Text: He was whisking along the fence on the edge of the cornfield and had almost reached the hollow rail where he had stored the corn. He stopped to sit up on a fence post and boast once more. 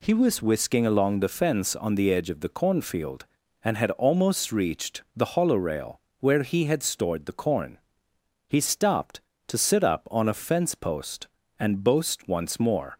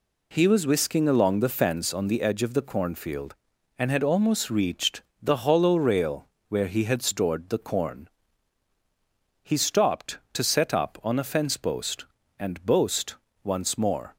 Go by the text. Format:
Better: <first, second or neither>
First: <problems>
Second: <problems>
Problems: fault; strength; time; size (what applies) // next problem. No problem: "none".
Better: first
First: pauses between "rail" and "where"; slight; at 5.9 s; 0.18 s long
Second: pauses between "reached" and "the"; slight; at 5.0 s; 0.20 s long // pauses between "rail" and "where"; slight; at 6.2 s; 0.22 s long // says "set" for "sit"; at 10.4 s // pauses between "boast" and "once"; slight; at 13.1 s; 0.28 s long